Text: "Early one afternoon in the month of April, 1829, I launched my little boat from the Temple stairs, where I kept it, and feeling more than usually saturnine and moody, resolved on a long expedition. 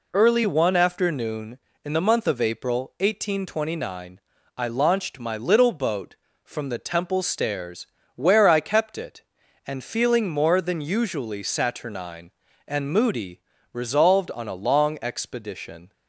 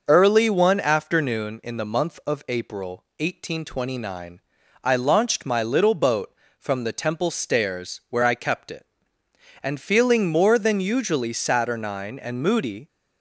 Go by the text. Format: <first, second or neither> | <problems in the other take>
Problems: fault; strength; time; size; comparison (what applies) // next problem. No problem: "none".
first | stops before "resolved on a long expedition"; at 12.8 s